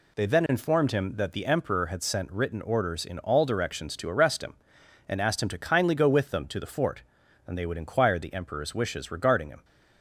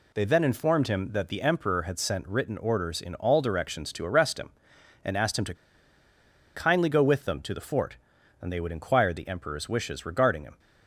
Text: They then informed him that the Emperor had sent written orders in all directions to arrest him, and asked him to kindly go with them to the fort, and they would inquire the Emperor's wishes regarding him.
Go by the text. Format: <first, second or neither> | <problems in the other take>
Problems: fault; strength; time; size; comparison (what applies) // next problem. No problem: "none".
first | pauses between "to" and "kindly"; at 5.5 s; 1.0 s long